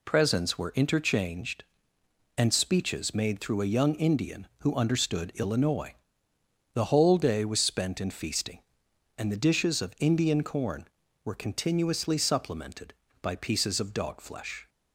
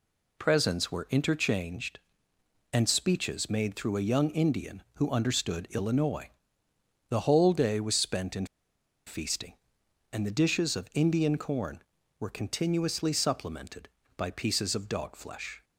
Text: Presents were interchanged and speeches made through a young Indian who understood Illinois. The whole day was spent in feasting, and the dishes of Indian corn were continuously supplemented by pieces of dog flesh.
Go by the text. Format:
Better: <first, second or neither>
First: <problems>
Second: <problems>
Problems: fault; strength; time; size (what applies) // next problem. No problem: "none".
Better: first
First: none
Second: pauses between "in" and "feasting"; noticeable; at 8.4 s; 0.61 s long